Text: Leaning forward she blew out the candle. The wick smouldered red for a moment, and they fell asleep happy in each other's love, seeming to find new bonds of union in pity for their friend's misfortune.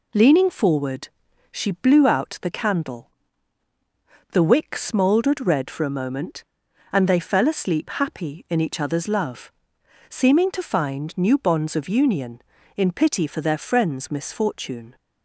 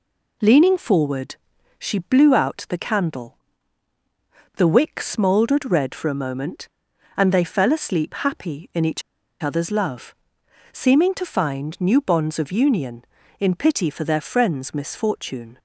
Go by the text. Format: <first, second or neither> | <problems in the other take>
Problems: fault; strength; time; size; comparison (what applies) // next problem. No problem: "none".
first | pauses between "forward" and "she"; noticeable; at 1.3 s; 0.46 s long; noticeable in the first // pauses between "each" and "other's"; at 9.0 s; 0.40 s long